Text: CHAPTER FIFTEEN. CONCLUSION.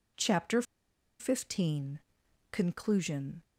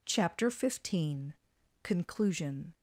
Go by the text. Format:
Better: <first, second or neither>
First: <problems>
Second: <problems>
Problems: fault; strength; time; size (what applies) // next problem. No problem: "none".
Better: second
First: pauses between "CHAPTER" and "FIFTEEN"; noticeable; at 0.6 s; 0.57 s long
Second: none